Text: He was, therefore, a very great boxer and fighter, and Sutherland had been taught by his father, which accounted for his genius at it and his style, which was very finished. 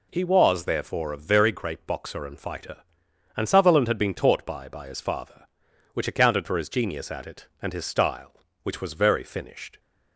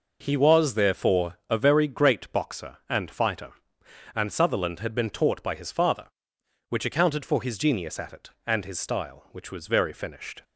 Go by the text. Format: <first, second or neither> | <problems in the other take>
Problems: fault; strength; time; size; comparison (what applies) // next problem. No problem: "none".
second | says "by" twice; at 4.6 s